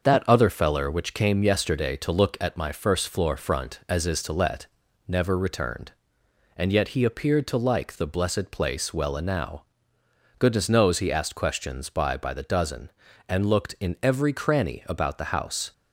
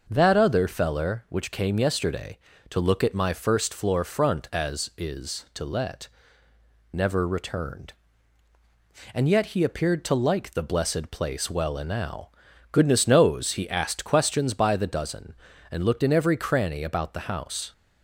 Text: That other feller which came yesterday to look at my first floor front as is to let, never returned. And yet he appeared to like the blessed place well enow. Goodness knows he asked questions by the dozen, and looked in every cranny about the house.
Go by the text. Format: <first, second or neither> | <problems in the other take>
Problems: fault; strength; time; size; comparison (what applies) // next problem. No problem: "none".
second | starts louder than the rest; until 1.0 s; 6.5 dB // says "by" twice; at 12.1 s